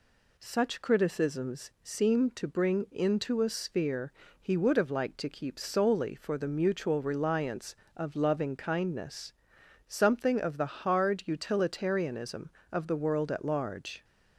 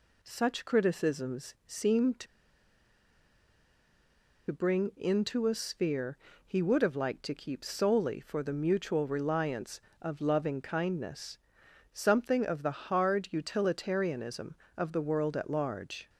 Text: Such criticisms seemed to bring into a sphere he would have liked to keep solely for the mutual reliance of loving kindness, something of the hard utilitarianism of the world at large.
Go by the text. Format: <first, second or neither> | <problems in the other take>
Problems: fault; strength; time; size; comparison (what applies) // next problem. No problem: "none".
first | pauses between "to" and "bring"; strong; at 2.2 s; 2.2 s long // pauses between "sphere" and "he"; slight; at 6.1 s; 0.28 s long; slight in the first